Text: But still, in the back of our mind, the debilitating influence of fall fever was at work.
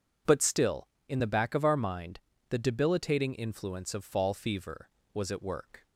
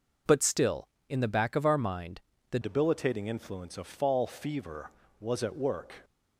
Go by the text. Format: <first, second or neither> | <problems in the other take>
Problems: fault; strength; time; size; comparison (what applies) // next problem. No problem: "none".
first | changes voice at "debilitating"; from 2.6 s on; 3.4 s long